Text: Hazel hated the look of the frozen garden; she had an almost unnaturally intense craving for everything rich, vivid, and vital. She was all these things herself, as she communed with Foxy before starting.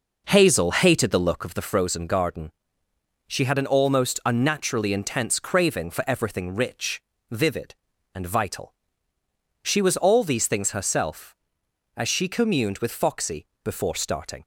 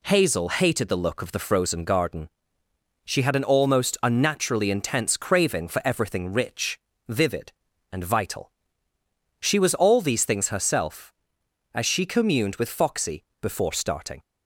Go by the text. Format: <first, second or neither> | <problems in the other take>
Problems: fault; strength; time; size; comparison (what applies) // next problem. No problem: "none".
second | starts louder than the rest; noticeable; until 1.4 s; 5 dB // pauses between "Foxy" and "before"; slight; at 13.4 s; 0.18 s long; slight in the second